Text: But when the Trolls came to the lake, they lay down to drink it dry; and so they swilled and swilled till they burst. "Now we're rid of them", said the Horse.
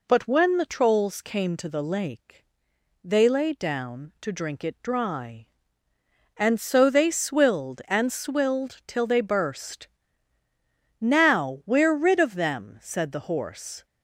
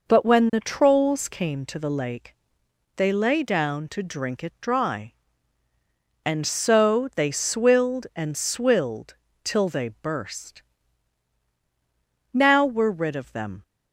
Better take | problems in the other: first | pauses between "swilled" and "till"; slight; at 9.1 s; 0.30 s long // stops before "said the Horse"; at 13.6 s

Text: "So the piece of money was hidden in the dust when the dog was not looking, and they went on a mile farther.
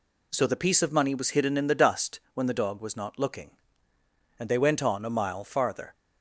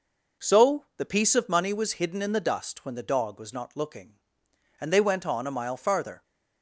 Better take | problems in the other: neither | none

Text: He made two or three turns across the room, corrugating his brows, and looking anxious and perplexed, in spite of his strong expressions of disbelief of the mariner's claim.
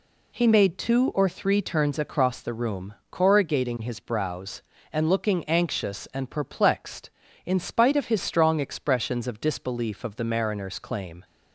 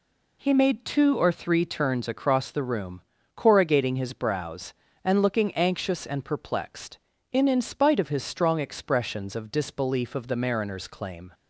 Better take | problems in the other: first | says "in" twice; at 7.4 s

